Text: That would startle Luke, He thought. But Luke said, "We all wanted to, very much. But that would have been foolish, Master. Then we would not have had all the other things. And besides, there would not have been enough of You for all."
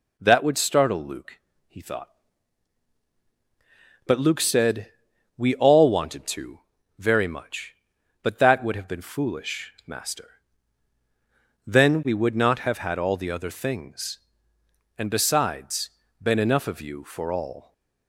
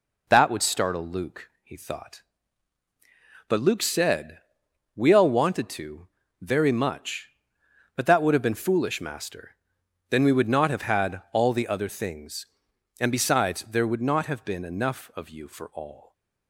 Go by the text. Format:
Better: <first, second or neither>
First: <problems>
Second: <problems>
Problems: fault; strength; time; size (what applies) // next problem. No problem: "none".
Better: second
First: skips "there would not have"; at 16.0 s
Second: none